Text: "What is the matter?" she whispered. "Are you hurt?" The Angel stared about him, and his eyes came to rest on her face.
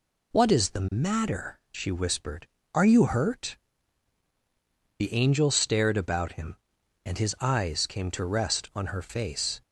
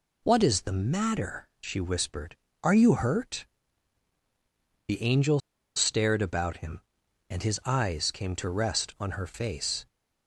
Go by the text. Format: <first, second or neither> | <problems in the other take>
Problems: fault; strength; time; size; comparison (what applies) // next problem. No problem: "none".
first | pauses between "Angel" and "stared"; slight; at 5.4 s; 0.36 s long